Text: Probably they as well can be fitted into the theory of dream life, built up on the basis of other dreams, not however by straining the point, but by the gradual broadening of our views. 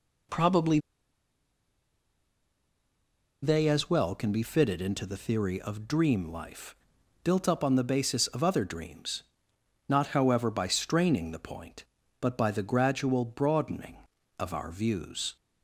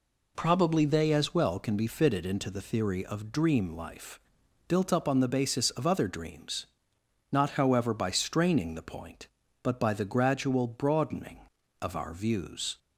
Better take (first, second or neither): second